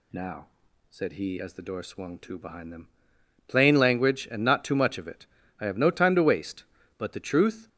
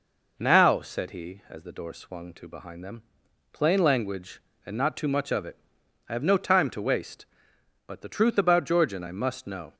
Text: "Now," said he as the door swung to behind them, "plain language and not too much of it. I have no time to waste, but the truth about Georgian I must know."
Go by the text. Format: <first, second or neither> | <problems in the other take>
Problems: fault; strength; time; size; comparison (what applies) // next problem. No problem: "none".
second | stops before "about Georgian I must know"; at 7.6 s